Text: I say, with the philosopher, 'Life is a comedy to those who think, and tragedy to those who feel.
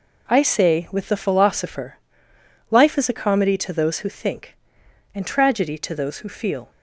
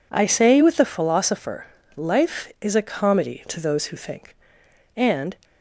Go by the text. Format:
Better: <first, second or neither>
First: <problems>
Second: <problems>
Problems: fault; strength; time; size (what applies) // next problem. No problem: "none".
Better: first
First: none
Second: stops before "tragedy to those who feel"; at 5.4 s